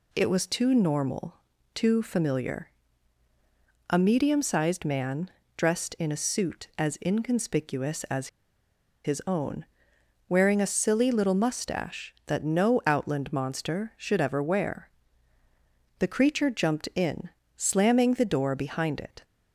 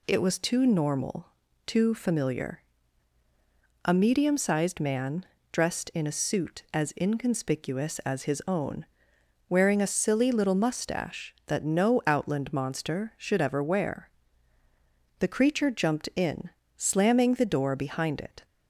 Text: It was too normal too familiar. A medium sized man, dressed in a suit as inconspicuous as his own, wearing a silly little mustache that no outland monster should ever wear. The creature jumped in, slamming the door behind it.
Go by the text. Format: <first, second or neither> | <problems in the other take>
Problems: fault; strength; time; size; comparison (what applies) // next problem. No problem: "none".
second | pauses between "normal" and "too"; at 1.3 s; 0.38 s long; also in the second // pauses between "as" and "his"; noticeable; at 8.2 s; 0.77 s long